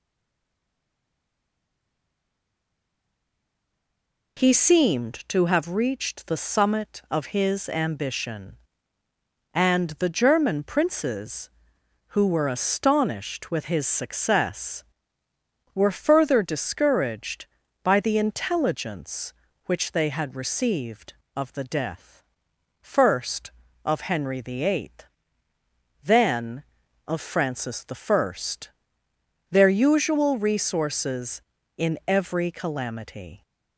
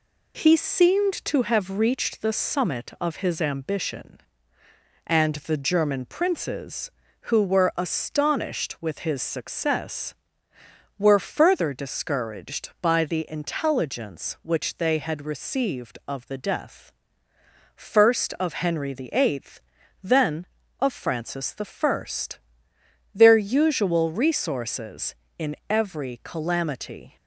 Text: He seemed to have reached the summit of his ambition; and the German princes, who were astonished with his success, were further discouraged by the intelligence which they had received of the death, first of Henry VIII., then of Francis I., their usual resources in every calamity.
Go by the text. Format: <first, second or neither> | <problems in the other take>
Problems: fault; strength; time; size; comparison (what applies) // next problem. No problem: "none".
second | stays silent before the first word; strong; until 4.3 s; 4.3 s long